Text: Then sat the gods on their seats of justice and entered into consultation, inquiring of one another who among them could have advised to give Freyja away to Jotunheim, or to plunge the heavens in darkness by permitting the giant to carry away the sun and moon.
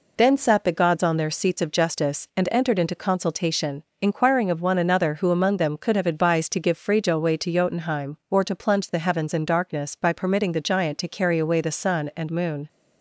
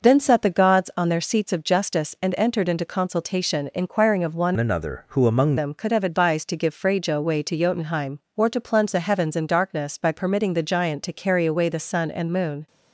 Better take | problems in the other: first | changes voice from "another" to "among"; from 4.5 to 5.5 s; 1.0 s long

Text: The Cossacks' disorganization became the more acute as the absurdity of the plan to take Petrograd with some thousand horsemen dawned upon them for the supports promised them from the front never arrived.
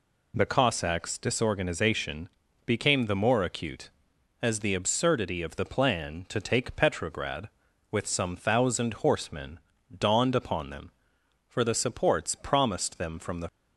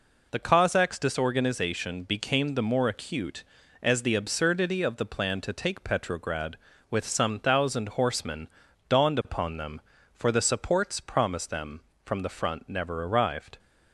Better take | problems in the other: second | pauses between "disorganization" and "became"; at 2.2 s; 0.38 s long // pauses between "horsemen" and "dawned"; slight; at 9.6 s; 0.36 s long; also in the second // stops before "front never arrived"; at 13.4 s

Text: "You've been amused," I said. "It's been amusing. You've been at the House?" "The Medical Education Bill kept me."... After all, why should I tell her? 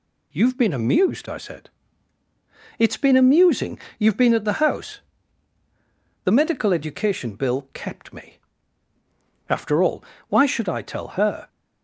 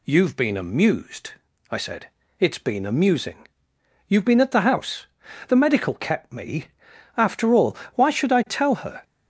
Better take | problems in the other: first | skips "Education Bill"; at 5.9 s

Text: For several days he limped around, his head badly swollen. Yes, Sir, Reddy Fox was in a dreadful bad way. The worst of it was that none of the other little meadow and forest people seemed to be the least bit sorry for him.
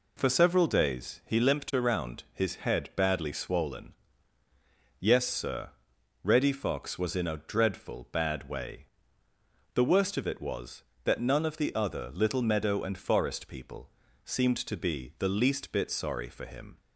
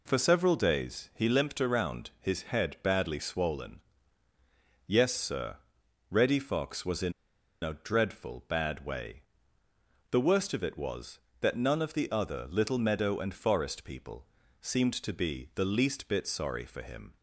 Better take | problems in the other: first | pauses between "in" and "a"; noticeable; at 7.1 s; 0.49 s long // pauses between "people" and "seemed"; slight; at 14.2 s; 0.34 s long; slight in the first

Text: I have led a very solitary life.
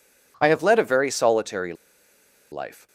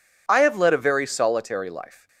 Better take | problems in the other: second | pauses between "solitary" and "life"; noticeable; at 1.7 s; 0.78 s long

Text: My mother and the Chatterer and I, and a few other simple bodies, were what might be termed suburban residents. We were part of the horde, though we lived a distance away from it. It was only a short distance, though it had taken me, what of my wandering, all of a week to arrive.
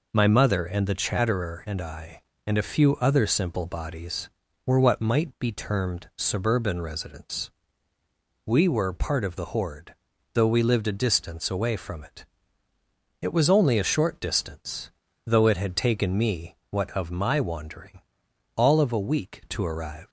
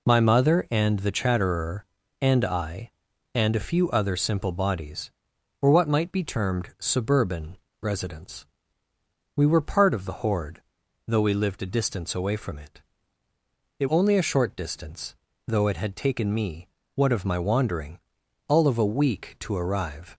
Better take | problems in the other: first | pauses between "suburban" and "residents"; slight; at 7.5 s; 0.24 s long // skips "was"; at 13.8 s

